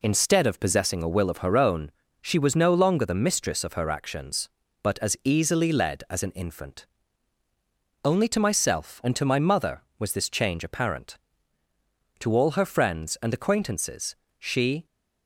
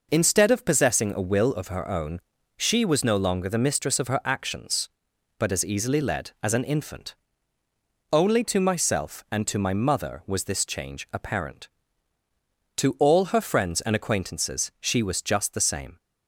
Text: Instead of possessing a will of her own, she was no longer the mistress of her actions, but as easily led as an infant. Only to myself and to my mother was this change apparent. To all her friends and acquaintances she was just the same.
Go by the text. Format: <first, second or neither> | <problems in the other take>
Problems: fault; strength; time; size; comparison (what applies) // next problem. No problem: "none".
second | pauses between "acquaintances" and "she"; slight; at 14.1 s; 0.24 s long // stops before "was just the same"; at 14.8 s